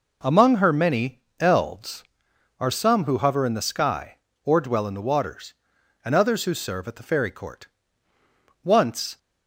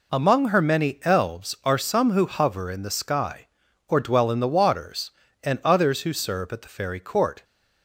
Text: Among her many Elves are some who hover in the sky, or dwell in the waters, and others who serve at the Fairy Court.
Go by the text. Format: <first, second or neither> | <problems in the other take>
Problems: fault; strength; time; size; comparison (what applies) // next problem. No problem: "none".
second | pauses between "many" and "Elves"; slight; at 1.1 s; 0.20 s long // goes on to say "Once"; from 8.6 s on; 0.54 s long